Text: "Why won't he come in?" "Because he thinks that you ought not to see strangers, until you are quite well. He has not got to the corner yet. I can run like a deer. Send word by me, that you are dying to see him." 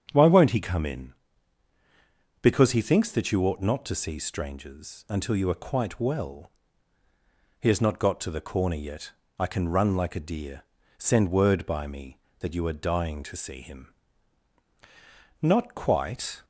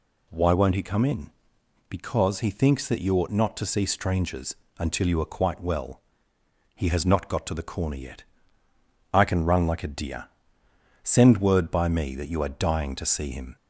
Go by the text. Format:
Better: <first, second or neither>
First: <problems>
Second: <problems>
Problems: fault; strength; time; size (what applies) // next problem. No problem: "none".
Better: second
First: starts louder than the rest; strong; until 1.1 s; 8 dB // goes on to say "Not quite"; noticeable; from 15.4 s on; 1.0 s long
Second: none